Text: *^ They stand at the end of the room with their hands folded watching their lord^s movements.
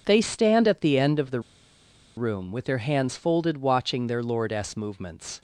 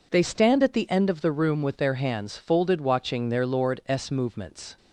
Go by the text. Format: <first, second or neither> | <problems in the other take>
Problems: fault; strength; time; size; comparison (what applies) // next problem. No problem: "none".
second | pauses between "the" and "room"; noticeable; at 1.3 s; 0.76 s long